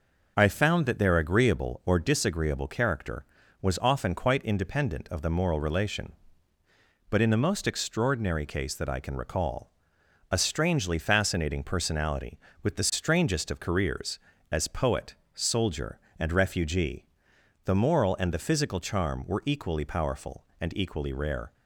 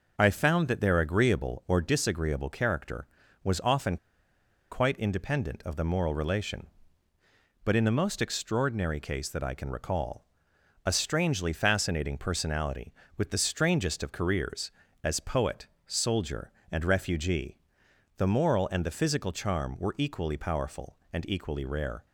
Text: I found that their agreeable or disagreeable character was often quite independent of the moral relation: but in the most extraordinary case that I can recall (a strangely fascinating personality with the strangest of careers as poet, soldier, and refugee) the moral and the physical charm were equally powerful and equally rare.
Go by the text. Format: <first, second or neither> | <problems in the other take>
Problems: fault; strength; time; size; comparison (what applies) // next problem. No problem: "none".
first | pauses between "often" and "quite"; noticeable; at 3.9 s; 0.74 s long